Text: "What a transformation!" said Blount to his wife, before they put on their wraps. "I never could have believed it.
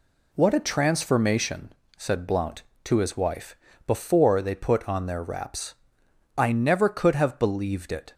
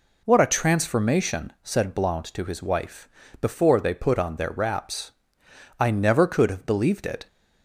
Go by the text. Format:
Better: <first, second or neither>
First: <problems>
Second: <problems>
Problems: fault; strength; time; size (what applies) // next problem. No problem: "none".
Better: neither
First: none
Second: none